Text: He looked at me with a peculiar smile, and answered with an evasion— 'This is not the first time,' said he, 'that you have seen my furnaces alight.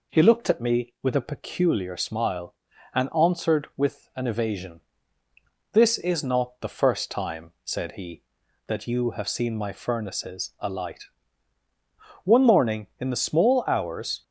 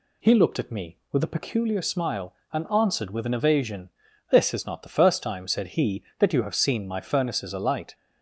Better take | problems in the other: second | goes on to say "One morning in the small hours"; strong; from 12.2 s on; 1.9 s long

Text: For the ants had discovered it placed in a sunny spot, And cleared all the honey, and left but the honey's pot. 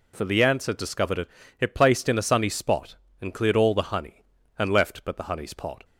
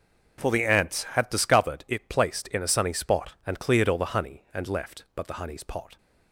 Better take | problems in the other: second | says "it" twice; at 1.5 s

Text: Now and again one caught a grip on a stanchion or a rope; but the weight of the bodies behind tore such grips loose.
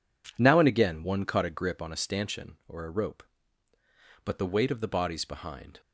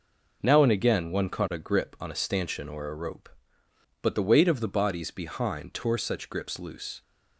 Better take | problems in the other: second | stops before "tore such grips loose"; at 5.7 s

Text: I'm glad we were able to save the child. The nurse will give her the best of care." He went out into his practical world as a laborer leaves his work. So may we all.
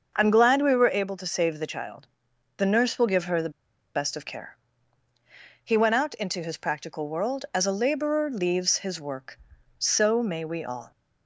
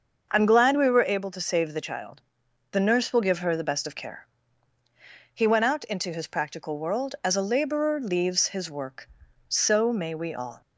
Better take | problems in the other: second | starts louder than the rest; until 1.1 s; 6.5 dB; also in the second // pauses between "the" and "best"; at 3.5 s; 0.44 s long

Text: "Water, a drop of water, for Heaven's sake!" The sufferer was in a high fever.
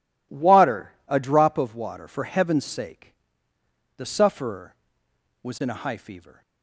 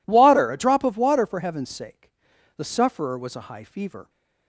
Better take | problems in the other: first | skips "in"; at 3.3 s

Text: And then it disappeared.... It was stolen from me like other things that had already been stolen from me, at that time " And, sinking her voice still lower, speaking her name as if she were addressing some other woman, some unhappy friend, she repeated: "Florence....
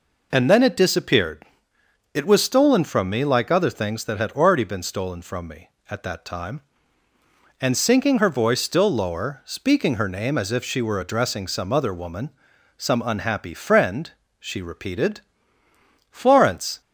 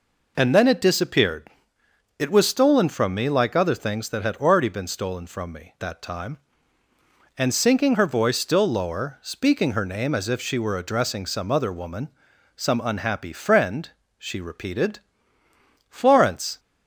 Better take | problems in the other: first | skips "at"; at 5.7 s

